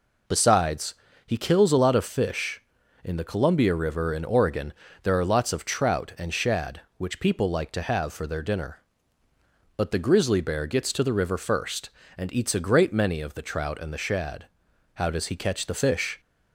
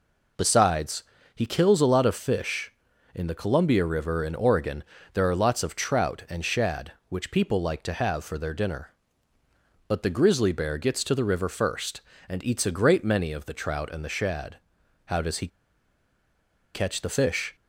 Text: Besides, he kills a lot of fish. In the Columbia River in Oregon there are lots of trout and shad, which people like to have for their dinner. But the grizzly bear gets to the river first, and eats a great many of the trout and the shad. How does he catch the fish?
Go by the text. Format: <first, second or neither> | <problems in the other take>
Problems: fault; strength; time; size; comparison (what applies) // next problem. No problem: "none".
first | pauses between "Oregon" and "there"; slight; at 4.8 s; 0.30 s long; slight in the first // pauses between "he" and "catch"; strong; at 15.4 s; 1.2 s long